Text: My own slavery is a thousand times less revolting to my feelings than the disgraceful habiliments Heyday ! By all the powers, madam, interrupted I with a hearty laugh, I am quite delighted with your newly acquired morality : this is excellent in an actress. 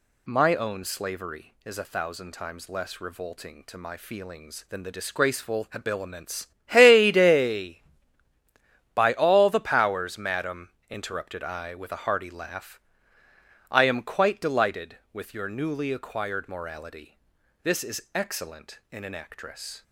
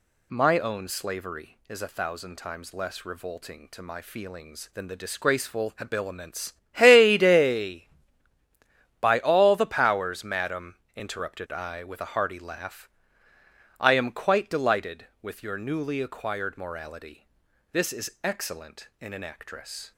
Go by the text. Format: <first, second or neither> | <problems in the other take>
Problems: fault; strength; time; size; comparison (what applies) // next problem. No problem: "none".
neither | pauses between "habiliments" and "Heyday"; slight; the same in both